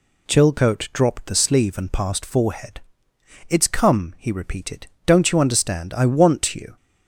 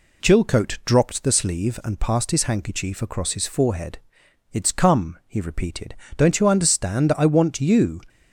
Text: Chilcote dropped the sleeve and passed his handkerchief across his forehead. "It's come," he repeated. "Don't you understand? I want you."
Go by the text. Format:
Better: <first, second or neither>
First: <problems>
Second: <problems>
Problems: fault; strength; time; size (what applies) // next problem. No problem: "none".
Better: second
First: skips "his handkerchief across his"; at 2.2 s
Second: none